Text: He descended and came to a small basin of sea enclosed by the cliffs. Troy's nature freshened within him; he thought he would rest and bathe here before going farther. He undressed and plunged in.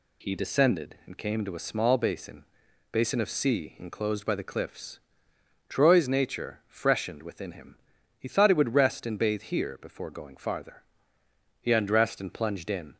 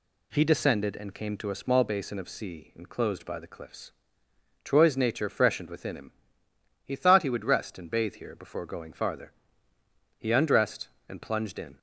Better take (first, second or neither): second